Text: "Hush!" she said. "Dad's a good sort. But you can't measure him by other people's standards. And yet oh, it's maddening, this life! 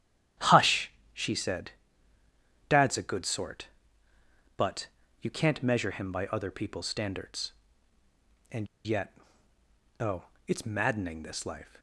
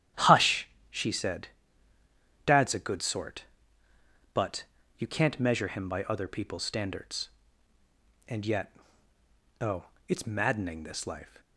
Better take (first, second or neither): second